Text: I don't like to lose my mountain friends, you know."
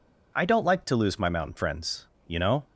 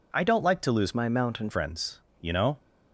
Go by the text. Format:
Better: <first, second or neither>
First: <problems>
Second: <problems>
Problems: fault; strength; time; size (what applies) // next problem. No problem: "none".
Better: first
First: none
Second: changes voice from "my" to "mountain"; from 0.9 to 1.4 s; 0.5 s long